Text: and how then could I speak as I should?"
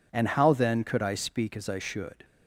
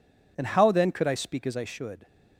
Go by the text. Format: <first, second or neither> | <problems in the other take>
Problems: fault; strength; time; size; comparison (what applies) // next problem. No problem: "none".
neither | none